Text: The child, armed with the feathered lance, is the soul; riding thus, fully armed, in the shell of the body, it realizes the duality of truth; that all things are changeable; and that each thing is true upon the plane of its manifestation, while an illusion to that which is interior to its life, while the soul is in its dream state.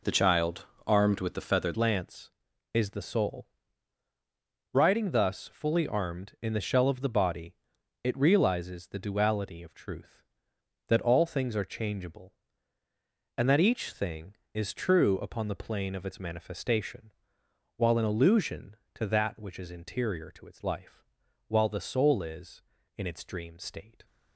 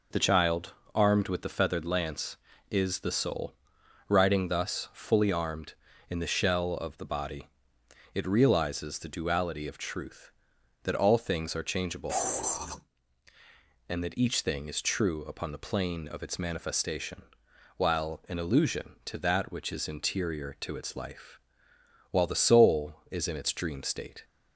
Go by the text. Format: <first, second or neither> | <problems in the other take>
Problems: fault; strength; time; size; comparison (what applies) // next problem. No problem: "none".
second | changes voice at "lance"; from 1.7 s on; 22.3 s long